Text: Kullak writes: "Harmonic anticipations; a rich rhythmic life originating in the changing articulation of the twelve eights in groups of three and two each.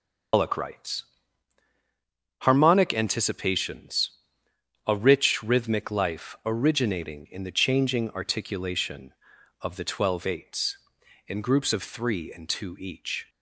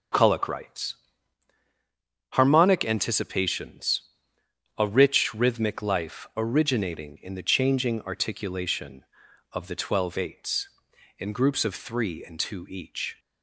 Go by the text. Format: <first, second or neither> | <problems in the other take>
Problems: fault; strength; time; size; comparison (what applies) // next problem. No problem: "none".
second | loses the start of "Kullak"; at 0.3 s; 125 ms // starts louder than the rest; until 2.7 s; 6.5 dB